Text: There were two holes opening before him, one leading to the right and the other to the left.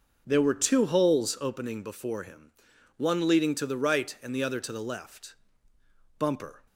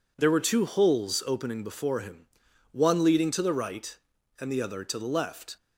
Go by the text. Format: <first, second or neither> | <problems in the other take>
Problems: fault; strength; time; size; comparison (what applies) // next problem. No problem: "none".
second | goes on to say "Bumper"; slight; from 6.1 s on; 0.44 s long